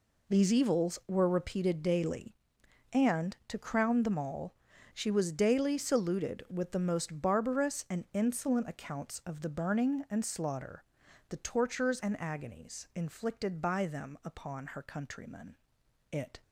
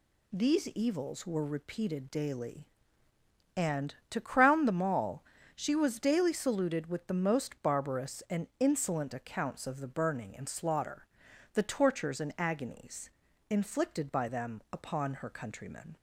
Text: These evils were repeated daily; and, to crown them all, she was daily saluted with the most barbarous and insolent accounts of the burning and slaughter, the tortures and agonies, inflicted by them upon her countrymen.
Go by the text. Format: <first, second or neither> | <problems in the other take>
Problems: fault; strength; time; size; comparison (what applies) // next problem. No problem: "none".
second | goes on to say "It"; slight; from 16.1 s on; 0.30 s long